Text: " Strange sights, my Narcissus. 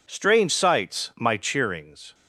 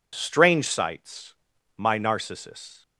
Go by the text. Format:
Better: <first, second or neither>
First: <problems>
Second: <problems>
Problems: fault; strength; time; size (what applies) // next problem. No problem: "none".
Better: second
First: says "Cheerings" for "Narcissus"; at 1.3 s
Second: none